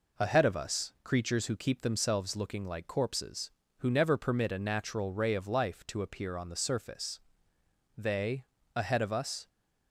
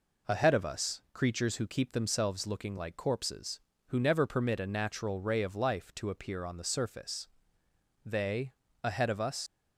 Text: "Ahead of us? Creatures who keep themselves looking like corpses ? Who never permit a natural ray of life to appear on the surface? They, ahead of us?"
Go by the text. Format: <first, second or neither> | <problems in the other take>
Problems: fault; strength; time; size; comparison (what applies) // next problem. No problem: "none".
first | leaves "us" unfinished; at 9.4 s; 95 ms